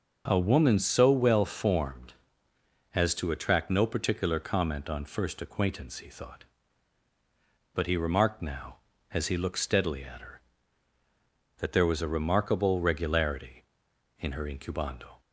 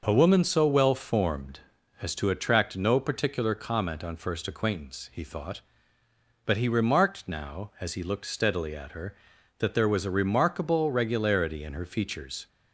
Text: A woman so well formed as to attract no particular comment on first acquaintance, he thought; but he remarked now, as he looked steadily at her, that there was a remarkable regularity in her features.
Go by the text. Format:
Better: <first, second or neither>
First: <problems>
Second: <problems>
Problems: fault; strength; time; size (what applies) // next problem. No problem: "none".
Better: second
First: says "incubando" for "features"; at 14.4 s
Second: none